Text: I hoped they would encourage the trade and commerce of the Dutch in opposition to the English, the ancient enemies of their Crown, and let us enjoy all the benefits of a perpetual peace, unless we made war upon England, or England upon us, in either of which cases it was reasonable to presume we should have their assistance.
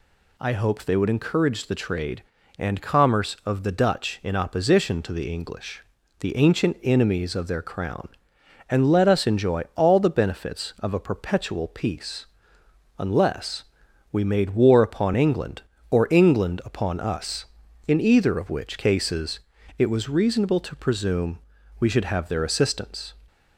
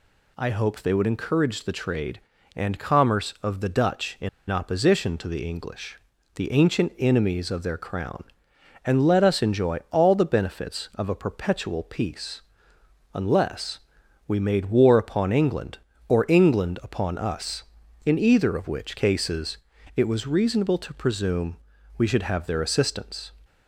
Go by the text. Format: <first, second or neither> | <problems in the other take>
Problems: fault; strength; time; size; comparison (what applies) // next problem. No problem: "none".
first | pauses between "in" and "opposition"; slight; at 4.2 s; 0.21 s long // pauses between "unless" and "we"; noticeable; at 13.7 s; 0.48 s long; noticeable in the first // pauses between "cases" and "it"; at 19.5 s; 0.40 s long; also in the first // pauses between "presume" and "we"; at 21.5 s; 0.40 s long; also in the first